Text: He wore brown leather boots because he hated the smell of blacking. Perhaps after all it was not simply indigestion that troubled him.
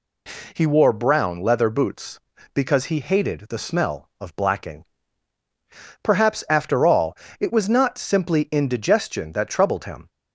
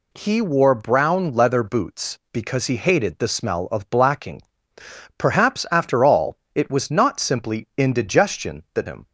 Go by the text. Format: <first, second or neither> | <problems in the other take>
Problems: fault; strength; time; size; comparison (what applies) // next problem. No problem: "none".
first | pauses between "all" and "it"; slight; at 6.3 s; 0.18 s long; slight in the first // skips "troubled"; at 8.8 s